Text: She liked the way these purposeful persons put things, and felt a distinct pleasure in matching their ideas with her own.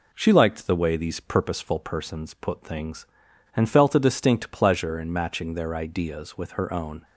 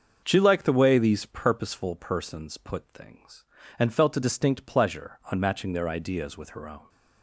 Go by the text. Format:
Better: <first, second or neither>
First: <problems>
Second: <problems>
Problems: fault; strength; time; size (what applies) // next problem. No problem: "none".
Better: first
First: none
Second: starts louder than the rest; until 1.2 s; 6.5 dB // says "on" for "in"; at 5.3 s